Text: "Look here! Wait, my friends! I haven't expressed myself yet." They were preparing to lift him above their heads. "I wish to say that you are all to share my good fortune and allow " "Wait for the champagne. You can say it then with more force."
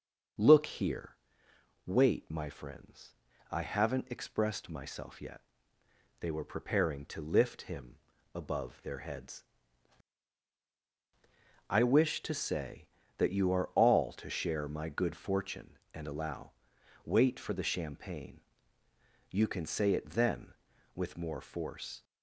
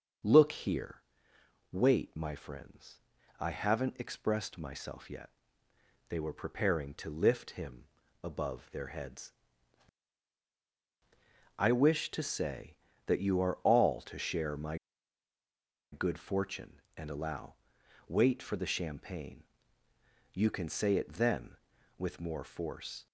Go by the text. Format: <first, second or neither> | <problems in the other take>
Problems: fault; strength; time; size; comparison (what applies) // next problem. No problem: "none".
first | starts louder than the rest; until 1.9 s; 6.5 dB; also in the first // pauses between "him" and "above"; at 7.8 s; 0.38 s long; also in the first // pauses between "my" and "good"; at 14.7 s; 1.1 s long